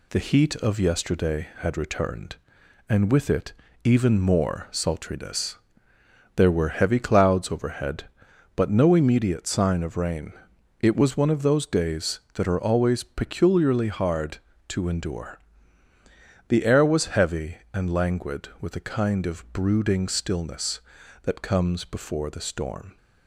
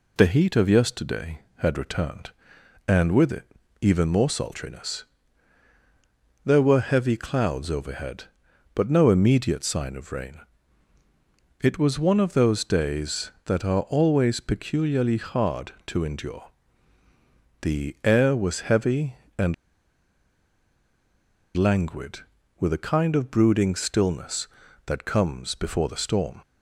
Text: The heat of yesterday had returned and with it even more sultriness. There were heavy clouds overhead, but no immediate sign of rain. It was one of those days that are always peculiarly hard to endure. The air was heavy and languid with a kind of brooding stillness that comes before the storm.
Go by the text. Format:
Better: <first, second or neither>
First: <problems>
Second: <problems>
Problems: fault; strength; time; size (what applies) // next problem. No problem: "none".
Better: first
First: pauses between "it" and "even"; slight; at 3.5 s; 0.31 s long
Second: pauses between "it" and "even"; slight; at 3.4 s; 0.36 s long // pauses between "and" and "languid"; strong; at 19.5 s; 2.0 s long